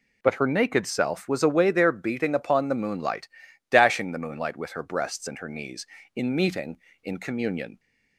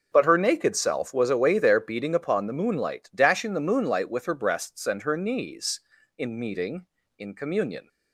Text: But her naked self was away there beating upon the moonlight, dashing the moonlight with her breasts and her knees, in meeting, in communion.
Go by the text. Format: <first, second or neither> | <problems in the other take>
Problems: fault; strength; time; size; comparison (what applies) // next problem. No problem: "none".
neither | none